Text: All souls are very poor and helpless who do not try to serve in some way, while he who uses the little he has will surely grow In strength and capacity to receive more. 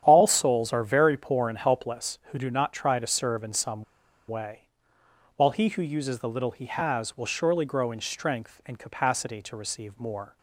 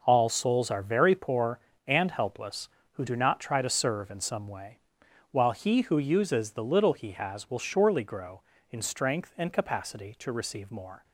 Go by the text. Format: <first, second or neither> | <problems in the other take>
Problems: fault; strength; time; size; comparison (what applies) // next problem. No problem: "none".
second | starts louder than the rest; strong; until 1.0 s; 9.5 dB // pauses between "some" and "way"; at 3.8 s; 0.45 s long